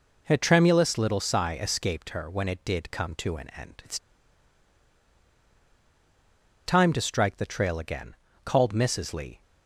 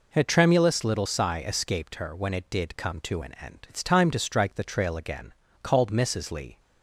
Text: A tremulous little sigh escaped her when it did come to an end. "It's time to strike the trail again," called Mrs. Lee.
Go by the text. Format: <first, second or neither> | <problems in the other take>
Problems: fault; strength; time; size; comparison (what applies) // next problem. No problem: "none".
second | pauses between "It's" and "time"; strong; at 3.9 s; 2.6 s long